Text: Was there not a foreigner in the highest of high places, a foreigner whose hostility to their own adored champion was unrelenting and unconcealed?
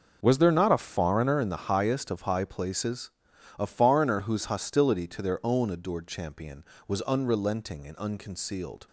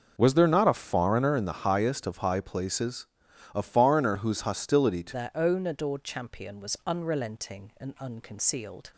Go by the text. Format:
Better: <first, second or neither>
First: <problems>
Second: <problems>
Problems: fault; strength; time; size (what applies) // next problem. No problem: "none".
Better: first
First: starts louder than the rest; noticeable; until 1.2 s; 6 dB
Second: starts louder than the rest; noticeable; until 1.1 s; 6 dB // changes voice at "their"; from 5.1 s on; 3.8 s long